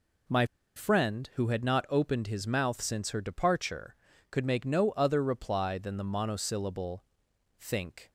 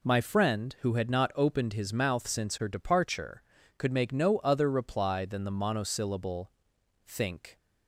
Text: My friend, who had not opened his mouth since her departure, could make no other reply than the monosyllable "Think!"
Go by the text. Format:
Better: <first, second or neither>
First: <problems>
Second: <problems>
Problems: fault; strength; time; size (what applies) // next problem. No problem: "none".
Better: second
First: pauses between "My" and "friend"; slight; at 0.4 s; 0.31 s long // pauses between "monosyllable" and "Think"; noticeable; at 7.0 s; 0.54 s long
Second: pauses between "monosyllable" and "Think"; noticeable; at 6.5 s; 0.54 s long